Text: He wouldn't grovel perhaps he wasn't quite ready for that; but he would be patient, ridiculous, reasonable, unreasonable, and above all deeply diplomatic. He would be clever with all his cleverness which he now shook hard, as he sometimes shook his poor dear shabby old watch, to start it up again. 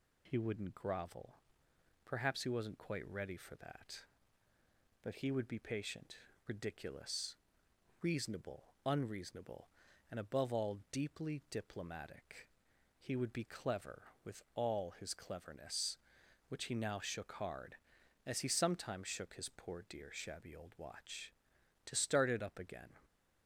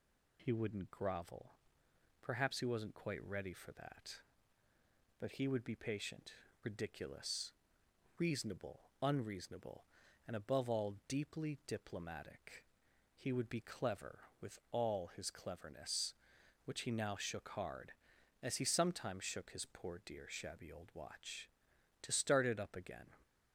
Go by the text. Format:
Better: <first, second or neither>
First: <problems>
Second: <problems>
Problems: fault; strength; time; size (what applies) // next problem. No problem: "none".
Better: neither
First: pauses between "grovel" and "perhaps"; noticeable; at 1.3 s; 0.68 s long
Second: pauses between "grovel" and "perhaps"; noticeable; at 1.5 s; 0.68 s long